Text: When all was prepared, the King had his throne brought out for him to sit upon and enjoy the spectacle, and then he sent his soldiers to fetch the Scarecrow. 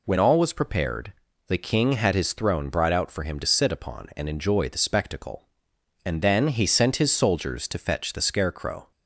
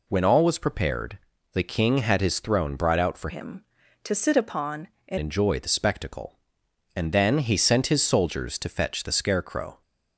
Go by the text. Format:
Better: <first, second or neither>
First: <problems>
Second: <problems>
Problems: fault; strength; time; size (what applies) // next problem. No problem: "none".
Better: first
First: none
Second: changes voice from "him" to "and"; from 3.2 to 5.1 s; 1.9 s long